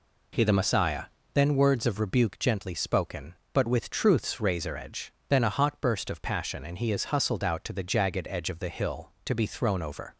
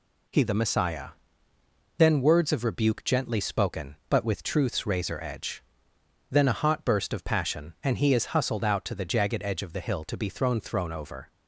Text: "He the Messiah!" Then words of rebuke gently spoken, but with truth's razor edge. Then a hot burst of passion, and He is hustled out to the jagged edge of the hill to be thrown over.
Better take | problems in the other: first | says "thrown" twice; at 10.5 s

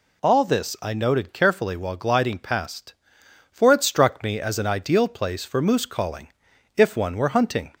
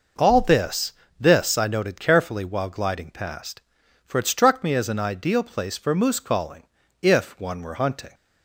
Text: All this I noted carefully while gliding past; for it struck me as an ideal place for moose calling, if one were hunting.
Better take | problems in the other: first | says "this" twice; at 1.1 s

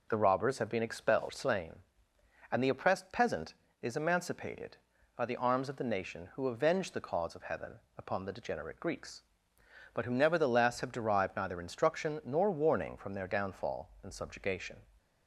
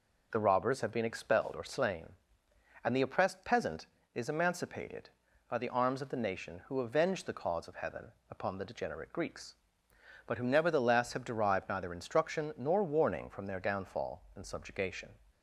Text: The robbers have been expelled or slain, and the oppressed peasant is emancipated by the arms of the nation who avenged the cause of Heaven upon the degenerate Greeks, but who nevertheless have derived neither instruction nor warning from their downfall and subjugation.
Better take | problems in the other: second | skips "or"; at 1.2 s // pauses between "Heaven" and "upon"; slight; at 7.7 s; 0.18 s long; slight in the second

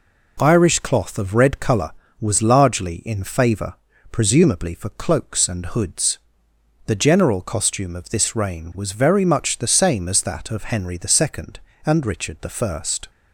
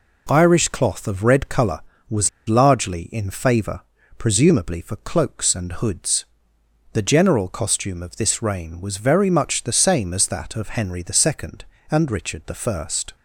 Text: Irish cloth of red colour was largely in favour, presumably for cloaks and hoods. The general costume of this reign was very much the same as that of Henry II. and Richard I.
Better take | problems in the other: first | pauses between "was" and "largely"; slight; at 2.2 s; 0.17 s long

